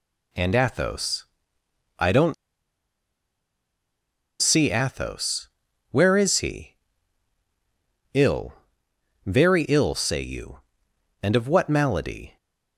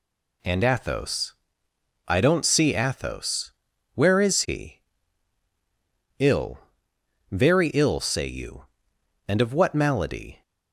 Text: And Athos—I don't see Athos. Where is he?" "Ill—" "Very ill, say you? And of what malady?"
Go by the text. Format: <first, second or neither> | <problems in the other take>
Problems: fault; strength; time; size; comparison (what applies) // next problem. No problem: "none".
second | pauses between "don't" and "see"; strong; at 2.3 s; 2.0 s long